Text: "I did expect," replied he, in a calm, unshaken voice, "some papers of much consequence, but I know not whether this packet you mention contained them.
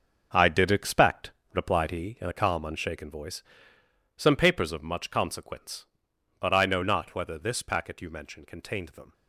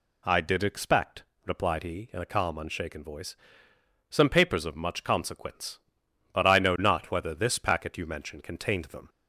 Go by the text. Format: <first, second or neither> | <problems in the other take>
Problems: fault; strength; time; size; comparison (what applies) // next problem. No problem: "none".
second | gets quieter; strong; throughout; 11 dB